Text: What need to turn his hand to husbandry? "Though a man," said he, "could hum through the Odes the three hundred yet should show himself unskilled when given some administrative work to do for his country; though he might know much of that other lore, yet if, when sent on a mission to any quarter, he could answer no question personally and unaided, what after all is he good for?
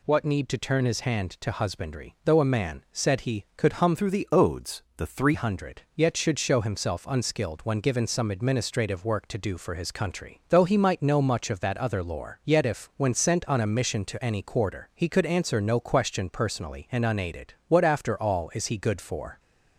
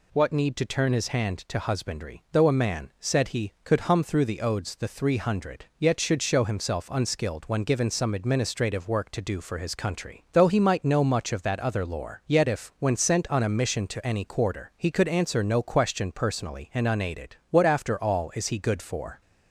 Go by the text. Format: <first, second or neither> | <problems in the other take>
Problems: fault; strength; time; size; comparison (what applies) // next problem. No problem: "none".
second | changes voice from "through" to "three"; from 3.9 to 5.3 s; 1.4 s long // pauses between "Odes" and "the"; slight; at 4.8 s; 0.16 s long